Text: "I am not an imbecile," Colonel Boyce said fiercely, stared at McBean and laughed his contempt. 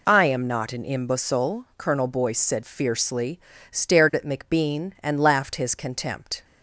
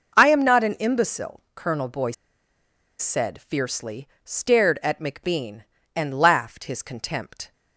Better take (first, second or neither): first